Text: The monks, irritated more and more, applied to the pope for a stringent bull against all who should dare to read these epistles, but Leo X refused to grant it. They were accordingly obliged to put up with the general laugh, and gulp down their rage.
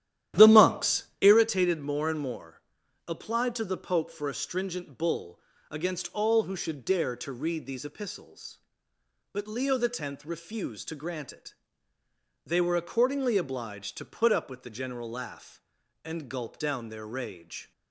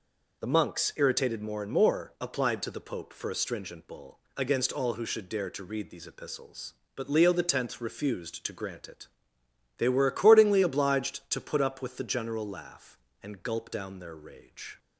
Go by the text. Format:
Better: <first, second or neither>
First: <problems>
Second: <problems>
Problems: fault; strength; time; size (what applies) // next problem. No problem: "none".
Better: second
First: starts louder than the rest; strong; until 1.4 s; 12 dB // pauses between "bull" and "against"; slight; at 5.3 s; 0.32 s long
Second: pauses between "bull" and "against"; slight; at 4.1 s; 0.16 s long